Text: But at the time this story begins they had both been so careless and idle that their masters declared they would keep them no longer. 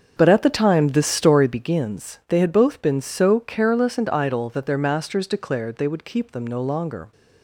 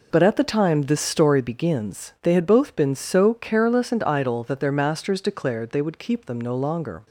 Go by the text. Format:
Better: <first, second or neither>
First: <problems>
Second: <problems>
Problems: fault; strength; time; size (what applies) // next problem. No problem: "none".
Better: second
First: starts louder than the rest; until 1.7 s; 7 dB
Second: none